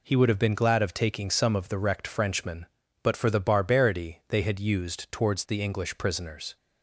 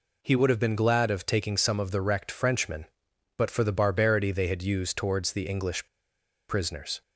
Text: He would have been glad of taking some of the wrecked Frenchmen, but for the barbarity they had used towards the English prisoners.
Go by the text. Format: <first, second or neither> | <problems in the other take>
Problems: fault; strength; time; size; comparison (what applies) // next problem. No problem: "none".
first | pauses between "English" and "prisoners"; noticeable; at 5.8 s; 0.62 s long